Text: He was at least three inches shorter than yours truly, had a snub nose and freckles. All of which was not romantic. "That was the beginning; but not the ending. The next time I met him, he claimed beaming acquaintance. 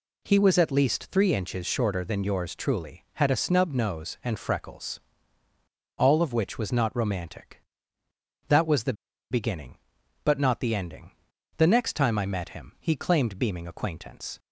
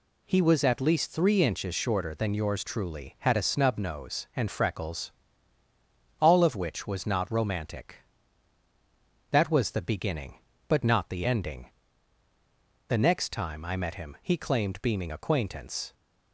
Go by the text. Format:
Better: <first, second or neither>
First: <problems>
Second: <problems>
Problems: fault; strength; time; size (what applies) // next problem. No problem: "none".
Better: second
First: pauses between "the" and "beginning"; at 8.9 s; 0.37 s long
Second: none